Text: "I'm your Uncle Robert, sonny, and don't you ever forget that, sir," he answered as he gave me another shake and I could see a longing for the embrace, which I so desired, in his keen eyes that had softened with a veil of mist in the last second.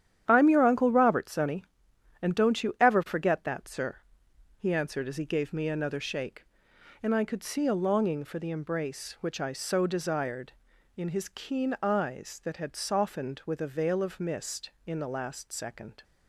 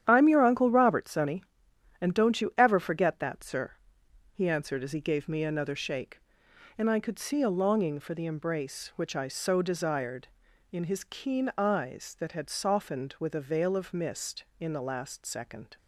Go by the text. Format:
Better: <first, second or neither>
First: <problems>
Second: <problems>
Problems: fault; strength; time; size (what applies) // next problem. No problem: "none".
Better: neither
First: starts louder than the rest; strong; until 1.2 s; 10 dB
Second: starts louder than the rest; strong; until 1.0 s; 10 dB